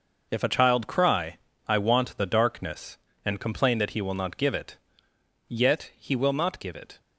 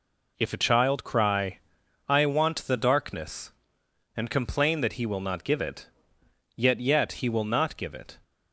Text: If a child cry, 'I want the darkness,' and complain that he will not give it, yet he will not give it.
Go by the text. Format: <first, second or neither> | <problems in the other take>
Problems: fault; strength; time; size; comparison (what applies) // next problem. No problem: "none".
first | says "yet" twice; at 6.7 s